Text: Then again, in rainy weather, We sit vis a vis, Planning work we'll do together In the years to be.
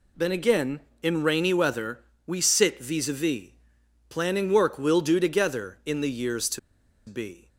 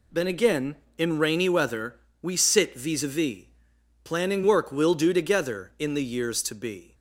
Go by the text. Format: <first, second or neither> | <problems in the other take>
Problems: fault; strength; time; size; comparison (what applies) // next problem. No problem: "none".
second | pauses between "to" and "be"; noticeable; at 6.5 s; 0.48 s long